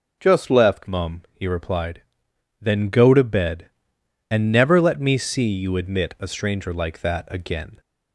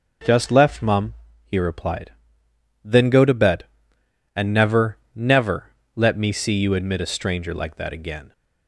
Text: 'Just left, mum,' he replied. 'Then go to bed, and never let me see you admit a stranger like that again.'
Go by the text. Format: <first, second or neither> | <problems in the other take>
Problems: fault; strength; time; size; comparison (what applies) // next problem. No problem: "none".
first | says "never" twice; at 5.1 s